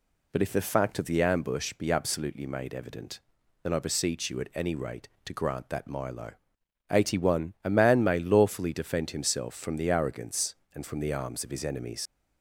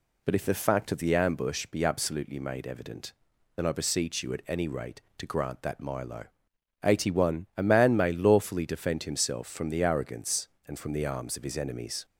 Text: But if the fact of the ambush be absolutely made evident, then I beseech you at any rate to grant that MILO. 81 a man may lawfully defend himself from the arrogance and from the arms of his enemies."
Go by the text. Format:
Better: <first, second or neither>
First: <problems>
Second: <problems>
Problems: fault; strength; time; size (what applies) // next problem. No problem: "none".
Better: second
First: leaves "enemies" unfinished; at 12.0 s; 65 ms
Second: none